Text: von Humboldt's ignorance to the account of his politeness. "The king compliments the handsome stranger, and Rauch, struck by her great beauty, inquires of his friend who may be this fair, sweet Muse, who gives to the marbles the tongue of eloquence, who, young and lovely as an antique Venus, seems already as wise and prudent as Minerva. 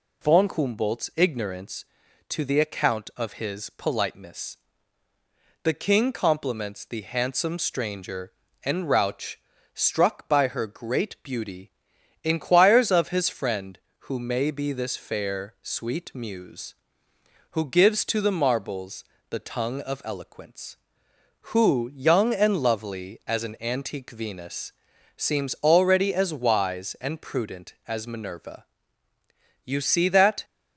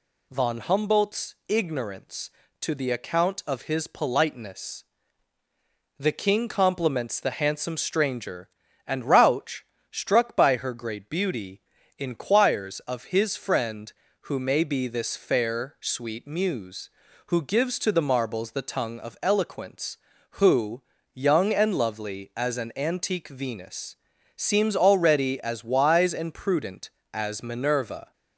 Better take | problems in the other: second | pauses between "marbles" and "the"; slight; at 19.0 s; 0.26 s long // goes on to say "You see that"; noticeable; from 29.6 s on; 0.80 s long

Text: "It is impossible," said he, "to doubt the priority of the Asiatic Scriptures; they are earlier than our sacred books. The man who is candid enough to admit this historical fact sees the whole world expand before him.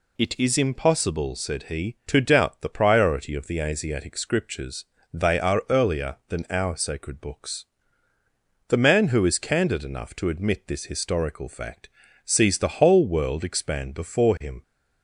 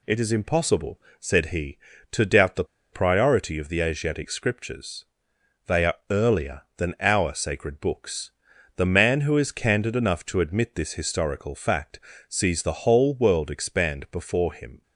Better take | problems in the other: first | pauses between "the" and "priority"; slight; at 2.6 s; 0.27 s long // pauses between "are" and "earlier"; slight; at 5.9 s; 0.16 s long // pauses between "fact" and "sees"; slight; at 11.9 s; 0.30 s long; slight in the first

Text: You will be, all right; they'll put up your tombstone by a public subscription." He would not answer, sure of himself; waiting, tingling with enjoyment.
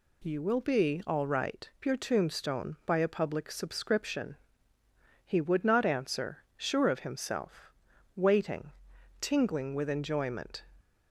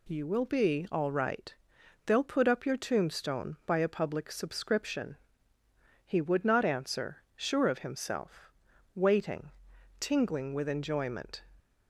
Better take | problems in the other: second | skips "they'll put up"; at 1.7 s

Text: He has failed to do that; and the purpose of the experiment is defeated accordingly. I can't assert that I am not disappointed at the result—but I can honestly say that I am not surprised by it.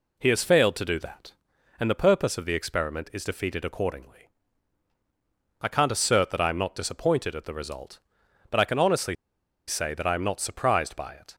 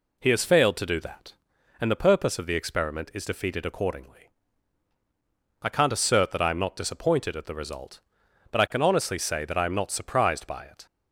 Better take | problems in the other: second | pauses between "honestly" and "say"; noticeable; at 9.1 s; 0.53 s long

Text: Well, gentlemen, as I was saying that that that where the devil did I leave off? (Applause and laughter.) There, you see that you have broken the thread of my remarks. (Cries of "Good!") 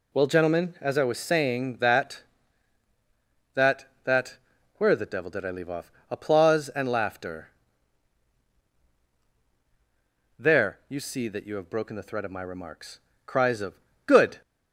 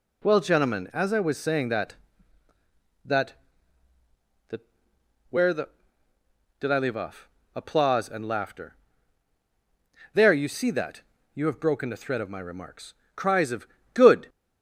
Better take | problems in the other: first | pauses between "that" and "where"; noticeable; at 4.6 s; 0.70 s long; also in the first // skips "devil"; at 6.1 s // pauses between "that" and "you"; slight; at 11.0 s; 0.34 s long // pauses between "of" and "Good"; slight; at 13.6 s; 0.28 s long; slight in the first

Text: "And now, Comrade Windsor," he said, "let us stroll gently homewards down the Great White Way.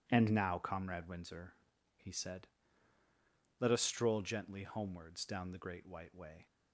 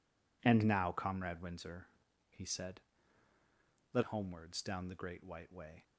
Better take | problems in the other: first | skips "us stroll gently"; at 4.0 s

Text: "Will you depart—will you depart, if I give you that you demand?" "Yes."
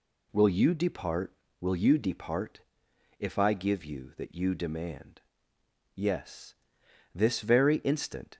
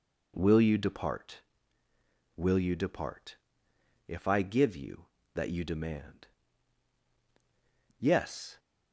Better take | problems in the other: second | goes on to say "This very instant"; noticeable; from 7.1 s on; 1.2 s long

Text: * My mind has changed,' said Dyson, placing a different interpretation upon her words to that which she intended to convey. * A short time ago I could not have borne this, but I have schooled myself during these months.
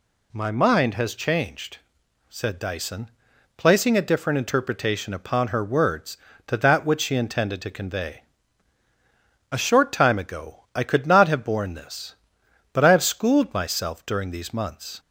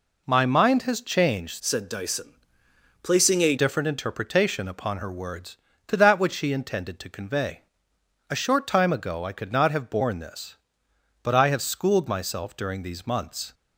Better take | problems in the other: first | changes voice from "said" to "a"; from 1.5 to 3.5 s; 2.0 s long

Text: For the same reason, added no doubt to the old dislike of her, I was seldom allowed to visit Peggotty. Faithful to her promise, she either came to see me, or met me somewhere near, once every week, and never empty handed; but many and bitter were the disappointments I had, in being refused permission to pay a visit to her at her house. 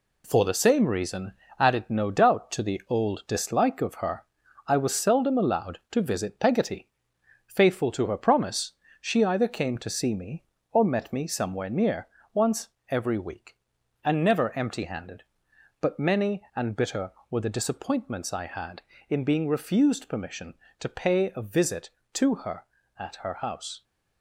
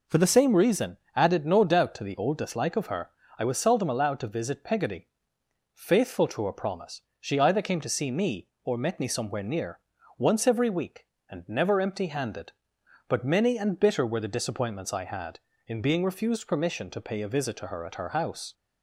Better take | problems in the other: second | gets quieter; throughout; 6.5 dB // pauses between "once" and "every"; slight; at 12.6 s; 0.20 s long

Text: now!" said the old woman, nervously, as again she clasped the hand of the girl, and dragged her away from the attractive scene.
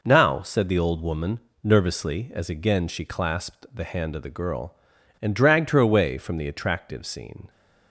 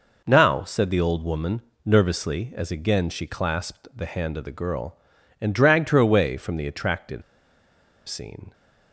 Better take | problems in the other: first | pauses between "attractive" and "scene"; noticeable; at 7.2 s; 0.85 s long

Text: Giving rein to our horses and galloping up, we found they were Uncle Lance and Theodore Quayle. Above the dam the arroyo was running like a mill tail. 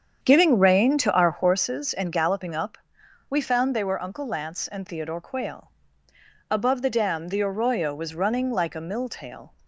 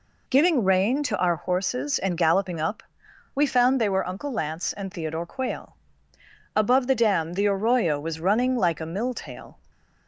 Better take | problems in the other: second | starts louder than the rest; strong; until 1.7 s; 8 dB

